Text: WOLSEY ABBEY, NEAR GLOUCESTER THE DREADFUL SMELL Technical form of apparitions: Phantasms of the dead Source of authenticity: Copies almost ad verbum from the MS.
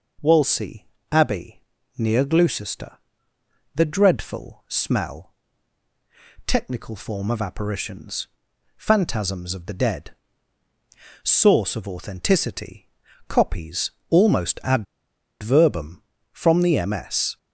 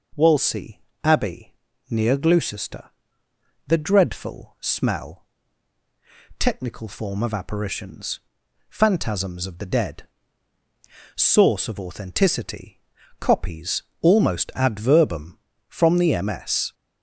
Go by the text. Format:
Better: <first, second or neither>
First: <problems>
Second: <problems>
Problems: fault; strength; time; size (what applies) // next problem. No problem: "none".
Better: second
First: pauses between "WOLSEY" and "ABBEY"; slight; at 0.8 s; 0.26 s long // pauses between "GLOUCESTER" and "THE"; noticeable; at 2.9 s; 0.76 s long // pauses between "SMELL" and "Technical"; at 5.3 s; 1.1 s long // pauses between "dead" and "Source"; at 10.0 s; 1.1 s long // pauses between "Copies" and "almost"; slight; at 13.9 s; 0.18 s long // pauses between "ad" and "verbum"; noticeable; at 14.8 s; 0.58 s long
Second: pauses between "WOLSEY" and "ABBEY"; slight; at 0.7 s; 0.24 s long // pauses between "GLOUCESTER" and "THE"; noticeable; at 2.9 s; 0.76 s long // pauses between "SMELL" and "Technical"; at 5.2 s; 1.1 s long // pauses between "dead" and "Source"; at 10.0 s; 1.1 s long // pauses between "Copies" and "almost"; slight; at 13.8 s; 0.18 s long